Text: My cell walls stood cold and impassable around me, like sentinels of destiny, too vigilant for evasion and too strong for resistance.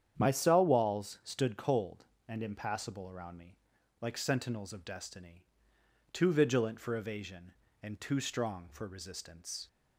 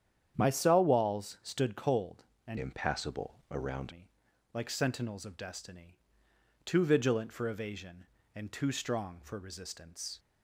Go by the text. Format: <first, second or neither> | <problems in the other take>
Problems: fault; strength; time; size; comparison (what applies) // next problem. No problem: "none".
first | starts louder than the rest; strong; until 1.3 s; 9 dB; strong in the first // changes voice from "impassable" to "around"; from 2.5 to 3.9 s; 1.4 s long